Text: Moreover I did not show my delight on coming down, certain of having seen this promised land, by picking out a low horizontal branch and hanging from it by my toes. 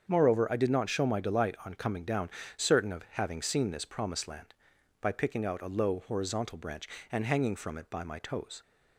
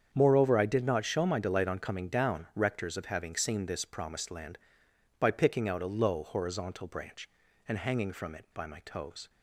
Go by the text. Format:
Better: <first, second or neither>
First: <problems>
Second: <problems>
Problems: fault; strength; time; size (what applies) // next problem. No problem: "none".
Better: first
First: starts louder than the rest; strong; until 1.0 s; 7 dB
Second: starts louder than the rest; strong; until 1.1 s; 7.5 dB // says "rectors" for "certain"; at 2.5 s